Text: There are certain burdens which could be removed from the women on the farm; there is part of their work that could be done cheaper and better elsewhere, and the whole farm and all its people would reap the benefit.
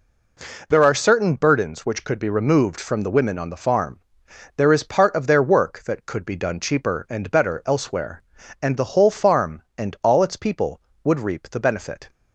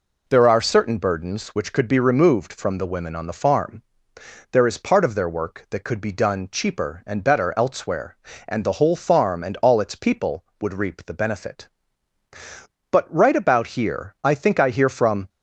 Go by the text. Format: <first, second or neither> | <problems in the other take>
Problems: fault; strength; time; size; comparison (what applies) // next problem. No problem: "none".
first | goes on to say "But right about here I think I hear from"; strong; from 12.9 s on; 2.3 s long